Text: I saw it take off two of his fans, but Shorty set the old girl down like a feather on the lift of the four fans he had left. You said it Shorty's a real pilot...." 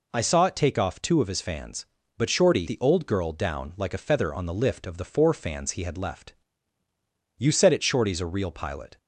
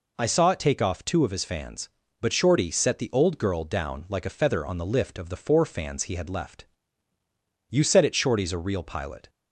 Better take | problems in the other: second | skips "set"; at 2.6 s

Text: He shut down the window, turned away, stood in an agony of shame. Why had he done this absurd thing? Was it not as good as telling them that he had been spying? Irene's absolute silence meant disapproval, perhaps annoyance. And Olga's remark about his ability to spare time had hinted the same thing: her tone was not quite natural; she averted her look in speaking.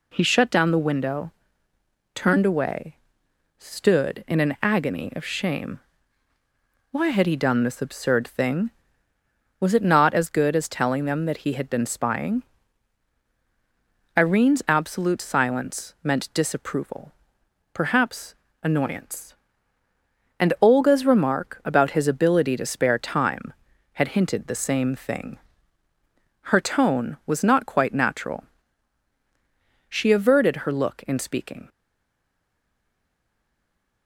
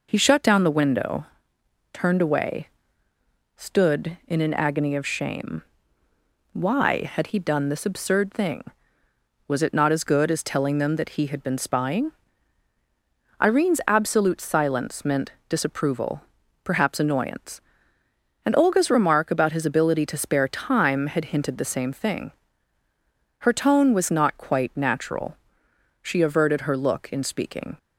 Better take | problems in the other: second | pauses between "perhaps" and "annoyance"; slight; at 18.3 s; 0.28 s long // stays silent after the last word; from 31.6 s on; 2.4 s long

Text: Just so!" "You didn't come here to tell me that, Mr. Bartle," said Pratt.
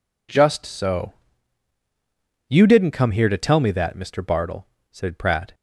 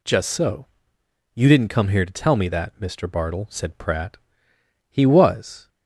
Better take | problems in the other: first | goes on to say "He was"; noticeable; from 4.8 s on; 0.80 s long

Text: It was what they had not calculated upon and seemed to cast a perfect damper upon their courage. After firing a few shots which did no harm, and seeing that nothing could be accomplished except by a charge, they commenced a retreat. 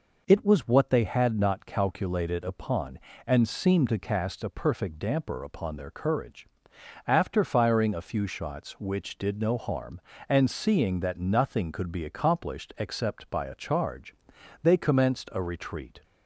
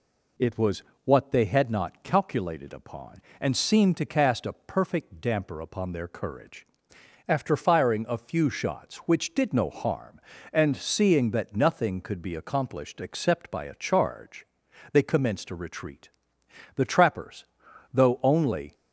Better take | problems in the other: first | pauses between "was" and "what"; slight; at 0.8 s; 0.20 s long // goes on to say "The trappers though only"; strong; from 16.7 s on; 1.9 s long

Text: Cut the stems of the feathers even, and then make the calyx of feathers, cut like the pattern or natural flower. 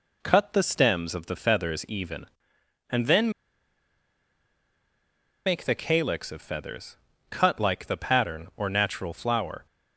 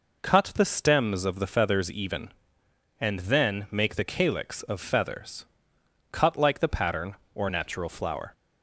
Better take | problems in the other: second | pauses between "then" and "make"; strong; at 3.3 s; 2.1 s long

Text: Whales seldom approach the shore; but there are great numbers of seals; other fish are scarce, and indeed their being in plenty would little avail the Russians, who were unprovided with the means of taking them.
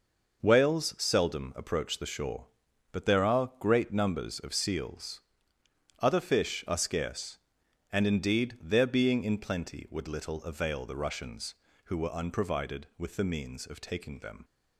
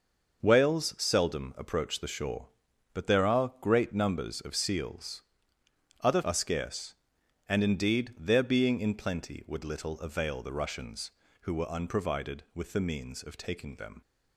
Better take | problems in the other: first | skips "fish"; at 6.2 s

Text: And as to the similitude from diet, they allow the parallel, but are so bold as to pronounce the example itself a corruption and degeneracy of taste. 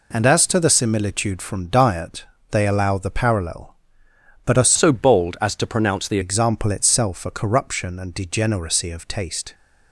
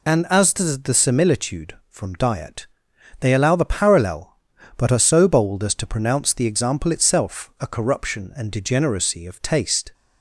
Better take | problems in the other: second | changes voice from "so" to "the"; from 4.7 to 6.1 s; 1.4 s long

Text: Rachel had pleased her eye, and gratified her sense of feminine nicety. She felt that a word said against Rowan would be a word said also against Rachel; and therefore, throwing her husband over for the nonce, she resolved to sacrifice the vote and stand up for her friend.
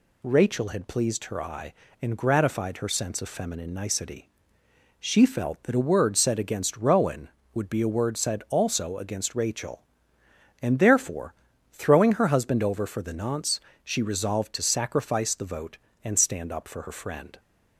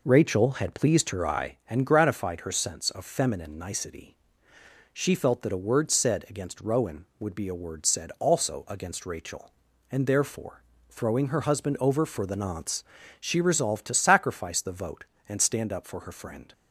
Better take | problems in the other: first | starts louder than the rest; noticeable; until 1.5 s; 4 dB

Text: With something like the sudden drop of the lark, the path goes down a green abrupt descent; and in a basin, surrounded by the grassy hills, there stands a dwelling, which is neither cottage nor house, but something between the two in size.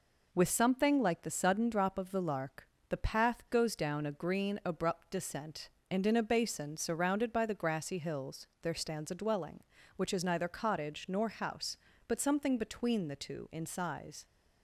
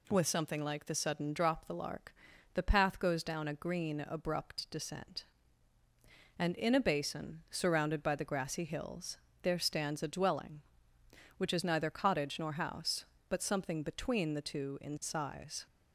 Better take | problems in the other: first | skips "of"; at 1.6 s

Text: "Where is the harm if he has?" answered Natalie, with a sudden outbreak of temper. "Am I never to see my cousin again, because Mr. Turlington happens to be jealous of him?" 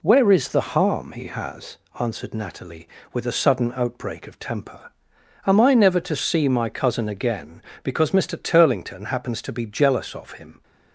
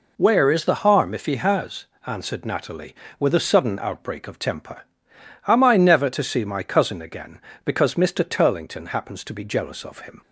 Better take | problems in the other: second | skips "if"; at 1.1 s

